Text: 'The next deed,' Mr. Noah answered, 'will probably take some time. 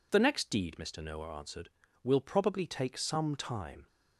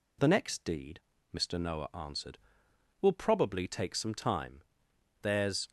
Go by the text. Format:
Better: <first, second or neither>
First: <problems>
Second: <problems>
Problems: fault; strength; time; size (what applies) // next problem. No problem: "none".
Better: first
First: none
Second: goes on to say "There's"; slight; from 5.2 s on; 0.48 s long